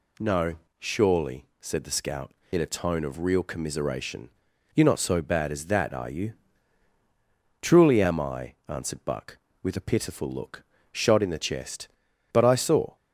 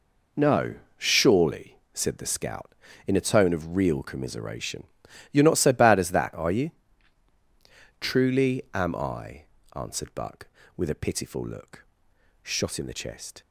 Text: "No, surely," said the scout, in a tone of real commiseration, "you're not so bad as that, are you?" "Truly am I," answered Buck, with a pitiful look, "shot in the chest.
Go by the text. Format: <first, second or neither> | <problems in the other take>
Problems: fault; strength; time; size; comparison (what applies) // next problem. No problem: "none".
second | goes on to say "But I saw"; noticeable; from 12.3 s on; 0.62 s long